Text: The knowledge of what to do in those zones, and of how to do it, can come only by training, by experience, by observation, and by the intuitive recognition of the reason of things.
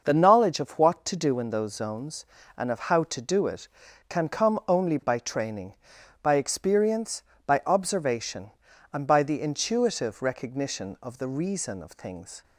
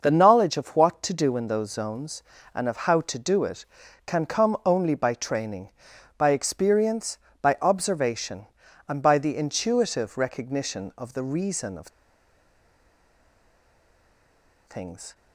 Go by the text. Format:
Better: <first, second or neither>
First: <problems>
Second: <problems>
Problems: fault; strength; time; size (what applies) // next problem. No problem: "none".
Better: first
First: none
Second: starts louder than the rest; noticeable; until 1.0 s; 6 dB // pauses between "of" and "things"; strong; at 11.8 s; 2.7 s long